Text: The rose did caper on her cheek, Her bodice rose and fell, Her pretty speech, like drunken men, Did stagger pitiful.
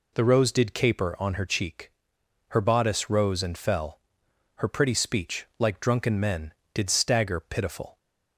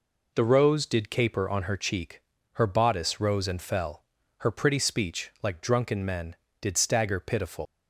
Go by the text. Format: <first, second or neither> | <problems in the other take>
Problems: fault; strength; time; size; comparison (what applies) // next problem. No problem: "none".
first | leaves "pitiful" unfinished; at 7.6 s; 130 ms